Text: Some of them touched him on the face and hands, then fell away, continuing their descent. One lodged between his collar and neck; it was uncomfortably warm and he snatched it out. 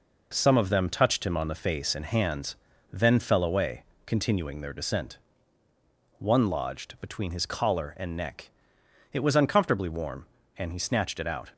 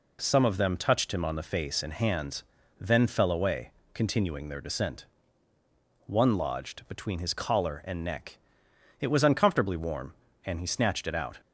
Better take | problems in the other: second | gets quieter; noticeable; throughout; 5 dB

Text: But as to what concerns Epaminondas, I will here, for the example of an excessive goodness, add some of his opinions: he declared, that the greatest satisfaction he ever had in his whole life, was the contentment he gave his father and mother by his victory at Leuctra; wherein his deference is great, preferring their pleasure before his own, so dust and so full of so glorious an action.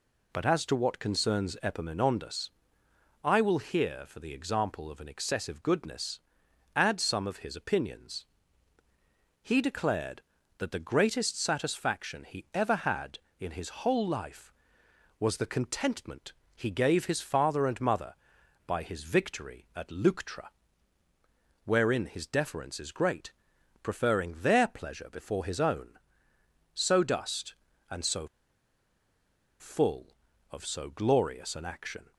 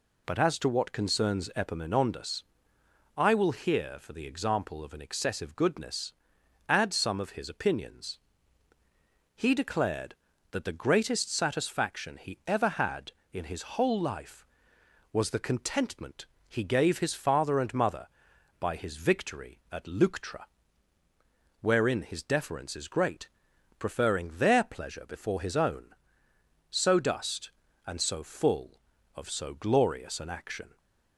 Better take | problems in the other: second | pauses between "contentment" and "he"; slight; at 16.3 s; 0.20 s long; slight in the second // pauses between "so" and "full"; strong; at 28.2 s; 1.3 s long

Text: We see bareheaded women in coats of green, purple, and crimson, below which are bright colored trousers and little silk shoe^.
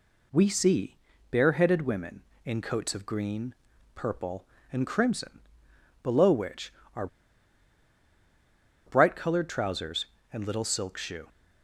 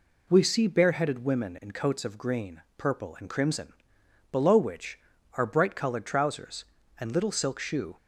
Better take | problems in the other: second | pauses between "see" and "bareheaded"; slight; at 0.9 s; 0.34 s long // pauses between "are" and "bright"; strong; at 7.0 s; 1.7 s long

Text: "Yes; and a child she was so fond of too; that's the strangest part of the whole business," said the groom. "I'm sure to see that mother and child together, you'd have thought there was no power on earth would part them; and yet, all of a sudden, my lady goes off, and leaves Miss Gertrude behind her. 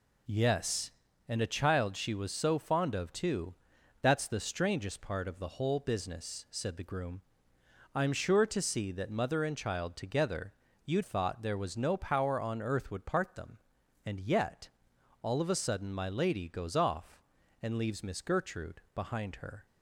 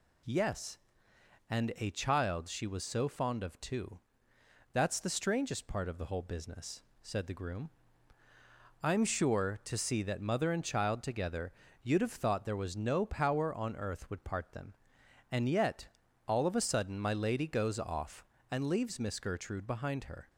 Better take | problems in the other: second | skips "have"; at 11.0 s

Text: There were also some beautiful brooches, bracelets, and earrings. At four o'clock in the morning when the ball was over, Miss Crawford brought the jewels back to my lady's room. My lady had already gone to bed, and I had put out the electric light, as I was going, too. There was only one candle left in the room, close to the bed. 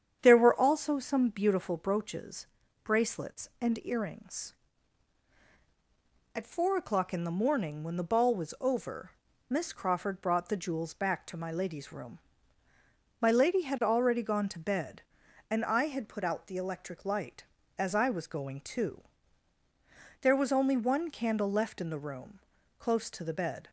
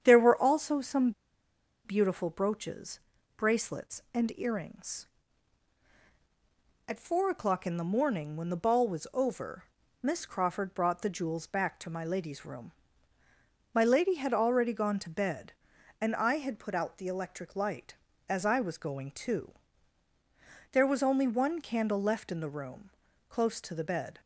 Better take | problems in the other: first | starts louder than the rest; strong; until 1.0 s; 8.5 dB; strong in the first // pauses between "some" and "beautiful"; noticeable; at 1.1 s; 0.73 s long

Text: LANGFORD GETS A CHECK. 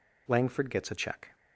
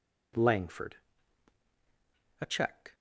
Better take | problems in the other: first | skips "GETS"; at 1.6 s

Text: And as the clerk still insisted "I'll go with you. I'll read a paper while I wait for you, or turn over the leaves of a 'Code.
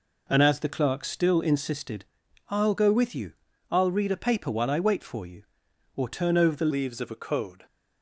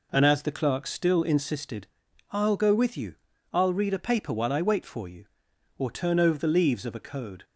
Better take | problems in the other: second | pauses between "insisted" and "I'll"; noticeable; at 2.0 s; 0.46 s long; noticeable in the second // changes voice at "leaves"; from 6.7 s on; 0.9 s long

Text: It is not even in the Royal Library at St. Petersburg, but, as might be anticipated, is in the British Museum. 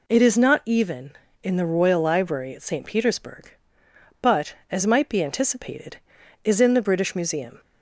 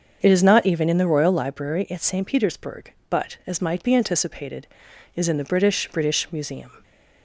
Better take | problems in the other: first | starts louder than the rest; until 1.2 s; 7 dB // says "British" twice; at 5.9 s

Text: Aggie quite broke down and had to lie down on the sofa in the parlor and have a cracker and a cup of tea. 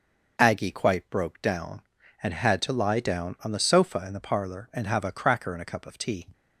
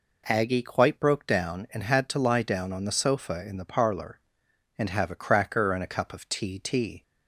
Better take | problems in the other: first | says "tea" twice; at 6.5 s

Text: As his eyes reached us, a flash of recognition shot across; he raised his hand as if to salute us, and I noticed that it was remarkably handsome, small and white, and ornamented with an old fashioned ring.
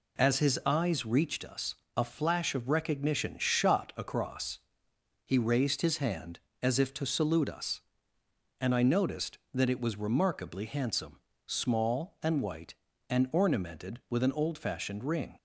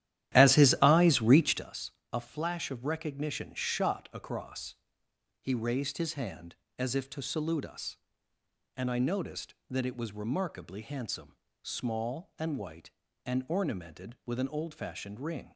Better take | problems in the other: first | starts louder than the rest; strong; until 1.8 s; 12.5 dB

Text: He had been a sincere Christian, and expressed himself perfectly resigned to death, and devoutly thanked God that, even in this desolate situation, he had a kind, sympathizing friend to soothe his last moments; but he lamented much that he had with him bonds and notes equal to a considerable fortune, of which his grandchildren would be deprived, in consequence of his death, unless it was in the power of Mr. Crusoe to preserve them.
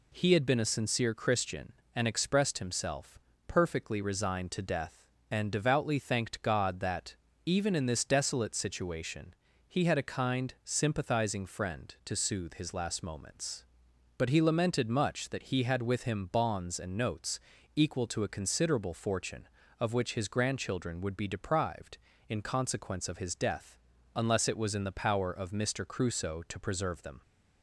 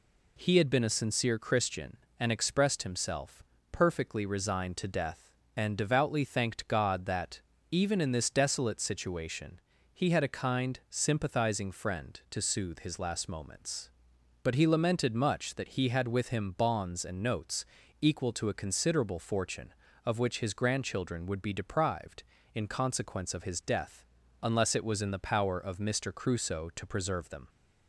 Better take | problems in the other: neither | pauses between "himself" and "perfectly"; slight; the same in both // pauses between "notes" and "equal"; slight; the same in both

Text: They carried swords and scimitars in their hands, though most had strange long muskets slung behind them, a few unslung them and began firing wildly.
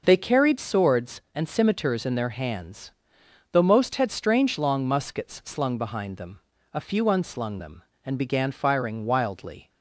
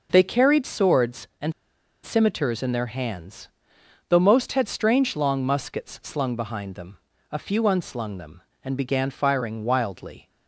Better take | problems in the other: first | pauses between "and" and "scimitars"; noticeable; at 1.5 s; 0.52 s long

